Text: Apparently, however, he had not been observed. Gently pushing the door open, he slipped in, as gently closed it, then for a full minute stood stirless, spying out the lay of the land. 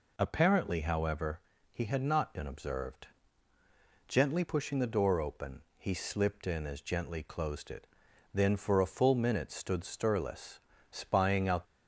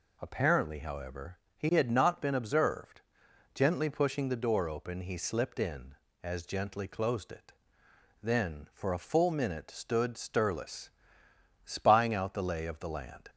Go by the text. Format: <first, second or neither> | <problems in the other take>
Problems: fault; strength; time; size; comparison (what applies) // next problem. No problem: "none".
second | stops before "the lay of the land"; at 11.6 s